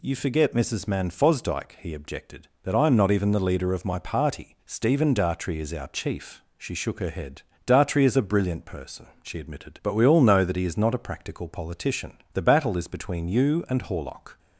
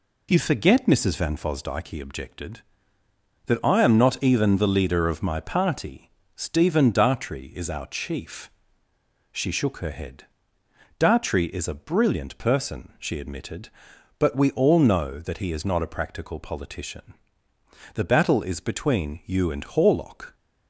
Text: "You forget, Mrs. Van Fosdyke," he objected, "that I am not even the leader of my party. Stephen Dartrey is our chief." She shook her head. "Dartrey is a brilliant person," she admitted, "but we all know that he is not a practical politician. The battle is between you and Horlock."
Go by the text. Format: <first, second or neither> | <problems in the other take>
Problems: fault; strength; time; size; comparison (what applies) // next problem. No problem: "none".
second | says "Man" for "Van"; at 0.8 s